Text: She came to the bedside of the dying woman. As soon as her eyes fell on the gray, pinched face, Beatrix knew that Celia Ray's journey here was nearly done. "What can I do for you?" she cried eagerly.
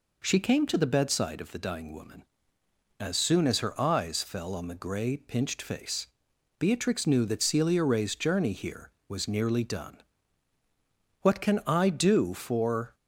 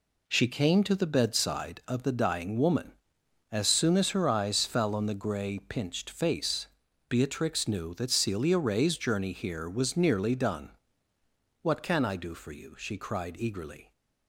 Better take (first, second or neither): second